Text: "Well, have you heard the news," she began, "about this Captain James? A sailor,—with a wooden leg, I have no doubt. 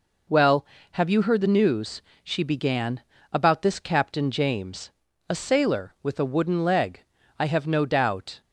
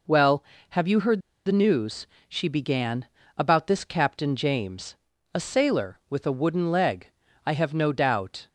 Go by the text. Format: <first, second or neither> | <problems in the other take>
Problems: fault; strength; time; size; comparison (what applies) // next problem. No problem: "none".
first | pauses between "heard" and "the"; slight; at 1.1 s; 0.27 s long